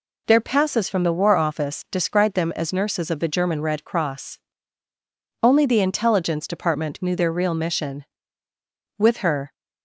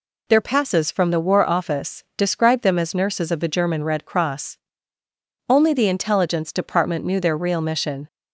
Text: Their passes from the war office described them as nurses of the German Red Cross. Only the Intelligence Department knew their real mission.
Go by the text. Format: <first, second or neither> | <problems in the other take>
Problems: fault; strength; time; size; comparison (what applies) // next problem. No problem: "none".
second | goes on to say "With her"; from 8.9 s on; 0.54 s long